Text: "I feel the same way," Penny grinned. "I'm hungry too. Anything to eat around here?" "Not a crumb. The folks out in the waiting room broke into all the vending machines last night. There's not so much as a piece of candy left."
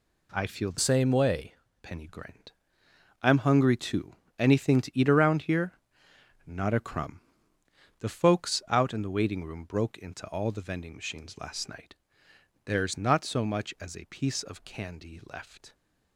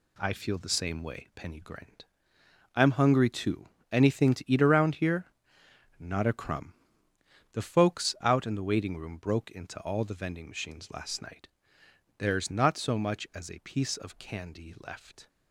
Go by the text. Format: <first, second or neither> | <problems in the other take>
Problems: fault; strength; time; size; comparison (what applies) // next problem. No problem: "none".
second | changes voice from "same" to "way"; from 0.7 to 1.5 s; 0.8 s long